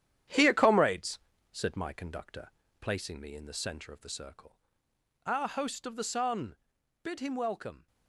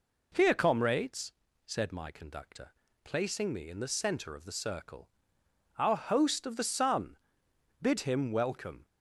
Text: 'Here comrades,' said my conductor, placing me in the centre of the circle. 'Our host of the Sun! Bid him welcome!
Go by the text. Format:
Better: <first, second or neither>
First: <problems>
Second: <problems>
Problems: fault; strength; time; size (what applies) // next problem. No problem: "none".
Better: second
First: gets quieter; noticeable; throughout; 6 dB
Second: none